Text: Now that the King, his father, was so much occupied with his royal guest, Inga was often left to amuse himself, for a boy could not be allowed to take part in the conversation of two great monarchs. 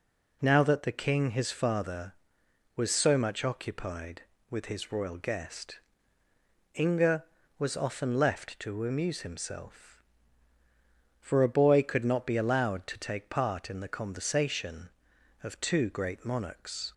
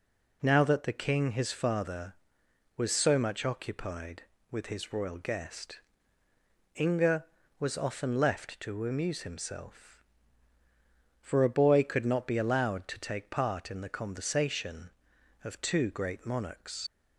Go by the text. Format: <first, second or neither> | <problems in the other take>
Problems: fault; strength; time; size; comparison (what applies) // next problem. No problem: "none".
first | leaves "monarchs" unfinished; at 16.8 s; 70 ms